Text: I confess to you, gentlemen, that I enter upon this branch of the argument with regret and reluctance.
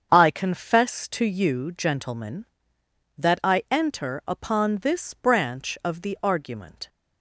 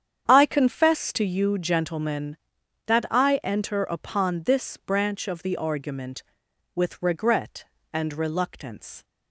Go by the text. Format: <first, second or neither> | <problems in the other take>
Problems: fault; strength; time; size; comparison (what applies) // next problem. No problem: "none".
second | starts louder than the rest; strong; until 1.1 s; 7.5 dB; strong in the second // stops before "with regret and reluctance"; at 6.8 s